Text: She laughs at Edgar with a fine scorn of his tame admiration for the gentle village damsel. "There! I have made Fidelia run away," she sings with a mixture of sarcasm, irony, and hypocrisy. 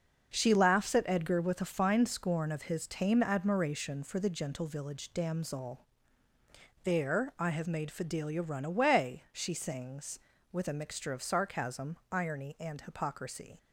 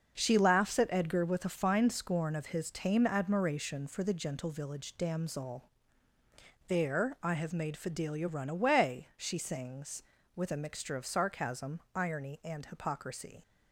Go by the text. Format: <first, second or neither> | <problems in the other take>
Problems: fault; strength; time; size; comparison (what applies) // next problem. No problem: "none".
neither | starts louder than the rest; the same in both